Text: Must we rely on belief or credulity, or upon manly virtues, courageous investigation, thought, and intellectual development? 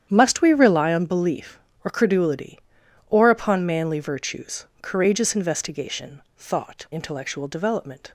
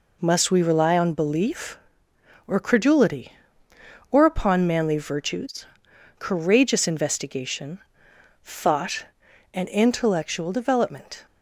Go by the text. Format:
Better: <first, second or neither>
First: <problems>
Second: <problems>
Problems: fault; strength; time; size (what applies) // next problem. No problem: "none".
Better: second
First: starts louder than the rest; strong; until 1.1 s; 9.5 dB // skips "and"; at 6.8 s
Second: none